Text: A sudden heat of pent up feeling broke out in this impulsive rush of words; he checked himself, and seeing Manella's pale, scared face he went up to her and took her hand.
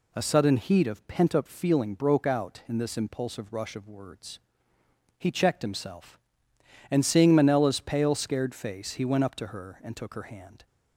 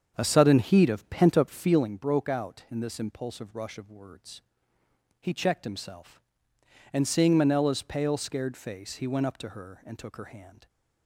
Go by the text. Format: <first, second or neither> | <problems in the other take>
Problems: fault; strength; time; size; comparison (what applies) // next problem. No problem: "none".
first | starts louder than the rest; strong; until 1.9 s; 7.5 dB